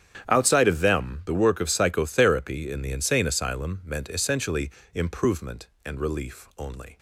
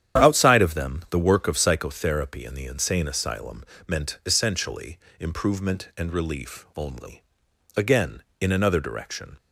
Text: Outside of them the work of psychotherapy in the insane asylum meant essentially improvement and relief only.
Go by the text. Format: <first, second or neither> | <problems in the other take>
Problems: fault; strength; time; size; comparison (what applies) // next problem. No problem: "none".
first | starts louder than the rest; strong; until 1.2 s; 9.5 dB; strong in the first // pauses between "asylum" and "meant"; slight; at 3.6 s; 0.24 s long // pauses between "essentially" and "improvement"; slight; at 4.9 s; 0.24 s long; slight in the first // goes on to say "Again in another direction"; from 7.7 s on; 1.6 s long